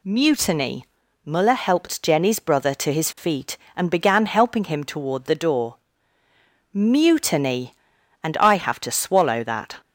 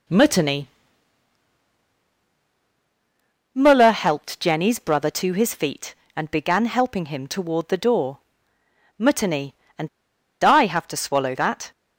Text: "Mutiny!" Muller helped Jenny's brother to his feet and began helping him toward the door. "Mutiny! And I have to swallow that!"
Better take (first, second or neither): first